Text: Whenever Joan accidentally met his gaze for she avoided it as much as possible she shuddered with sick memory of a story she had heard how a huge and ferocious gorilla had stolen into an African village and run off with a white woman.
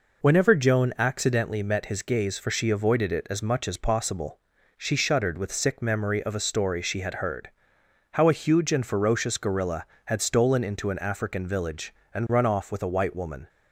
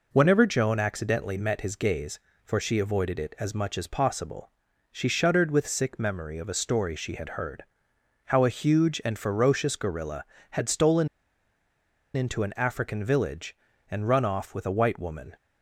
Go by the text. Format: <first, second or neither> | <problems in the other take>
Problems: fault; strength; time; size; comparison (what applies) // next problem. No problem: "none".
first | pauses between "possible" and "she"; at 4.4 s; 0.44 s long; also in the first // pauses between "heard" and "how"; noticeable; at 7.6 s; 0.62 s long; noticeable in the first // pauses between "stolen" and "into"; at 11.0 s; 1.0 s long